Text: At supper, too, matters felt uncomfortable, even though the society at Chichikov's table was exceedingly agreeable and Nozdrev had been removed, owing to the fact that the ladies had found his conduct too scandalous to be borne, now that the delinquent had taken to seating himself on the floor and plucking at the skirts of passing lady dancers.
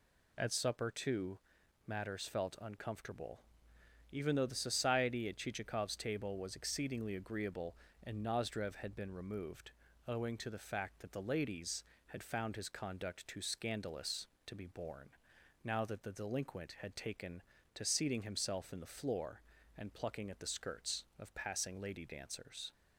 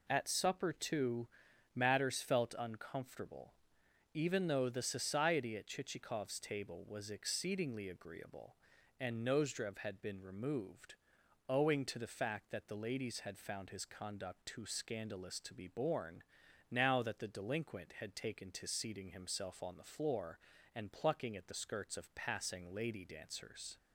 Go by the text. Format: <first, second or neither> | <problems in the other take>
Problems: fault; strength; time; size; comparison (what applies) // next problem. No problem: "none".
second | says "in" for "on"; at 18.7 s